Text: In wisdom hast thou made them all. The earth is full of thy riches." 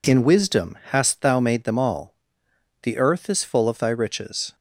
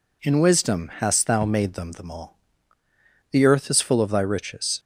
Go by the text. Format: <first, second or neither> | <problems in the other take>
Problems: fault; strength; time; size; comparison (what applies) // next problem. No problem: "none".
first | says "them" twice; at 1.9 s